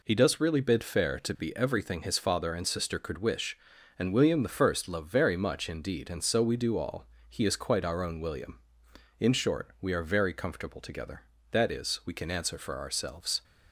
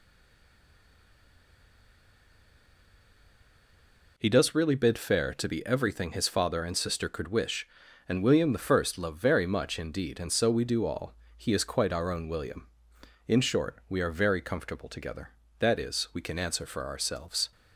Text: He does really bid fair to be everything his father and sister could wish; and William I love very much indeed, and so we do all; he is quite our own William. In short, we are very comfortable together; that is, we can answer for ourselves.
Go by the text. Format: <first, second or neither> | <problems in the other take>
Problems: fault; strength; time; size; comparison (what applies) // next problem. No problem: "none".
first | stays silent before the first word; strong; until 4.1 s; 4.1 s long